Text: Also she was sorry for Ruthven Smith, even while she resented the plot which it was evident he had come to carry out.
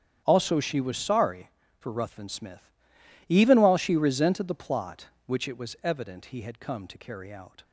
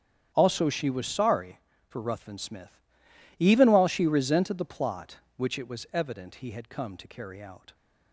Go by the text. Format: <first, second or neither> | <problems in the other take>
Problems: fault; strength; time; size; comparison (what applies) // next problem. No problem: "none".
neither | starts louder than the rest; strong; the same in both